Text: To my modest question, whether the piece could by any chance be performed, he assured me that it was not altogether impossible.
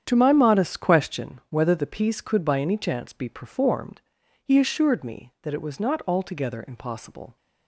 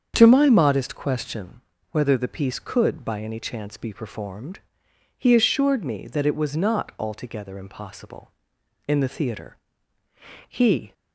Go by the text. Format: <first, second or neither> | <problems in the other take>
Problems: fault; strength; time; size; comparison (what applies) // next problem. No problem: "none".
first | starts louder than the rest; strong; until 1.1 s; 7.5 dB; strong in the first // goes on to say "In the theatre he"; strong; from 8.8 s on; 2.0 s long